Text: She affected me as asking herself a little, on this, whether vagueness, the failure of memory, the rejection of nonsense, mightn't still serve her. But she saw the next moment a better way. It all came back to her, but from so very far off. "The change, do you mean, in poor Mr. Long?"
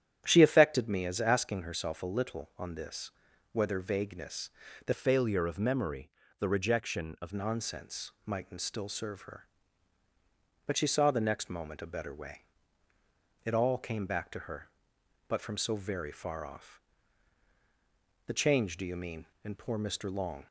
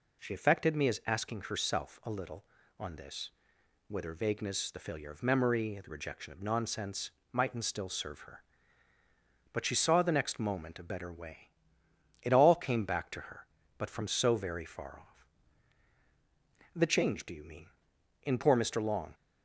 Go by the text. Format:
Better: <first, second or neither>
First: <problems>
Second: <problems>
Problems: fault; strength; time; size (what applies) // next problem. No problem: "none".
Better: second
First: starts louder than the rest; strong; until 1.2 s; 10 dB // changes voice from "failure" to "of"; from 4.9 to 7.3 s; 2.4 s long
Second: none